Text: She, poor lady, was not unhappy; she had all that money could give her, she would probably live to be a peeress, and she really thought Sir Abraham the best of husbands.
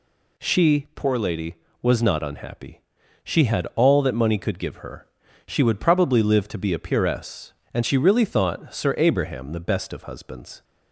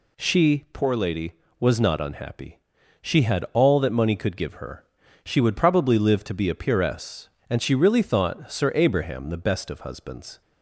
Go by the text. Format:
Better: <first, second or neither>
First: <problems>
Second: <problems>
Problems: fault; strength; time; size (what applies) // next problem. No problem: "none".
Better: neither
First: none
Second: none